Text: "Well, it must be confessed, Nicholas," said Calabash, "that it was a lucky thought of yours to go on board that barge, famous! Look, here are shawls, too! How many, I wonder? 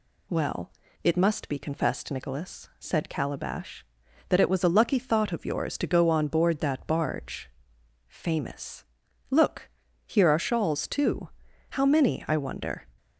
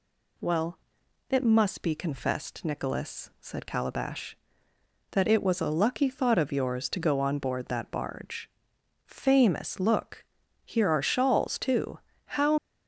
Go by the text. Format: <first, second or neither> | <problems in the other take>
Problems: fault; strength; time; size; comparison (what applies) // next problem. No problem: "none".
first | stops before "many I wonder"; at 12.5 s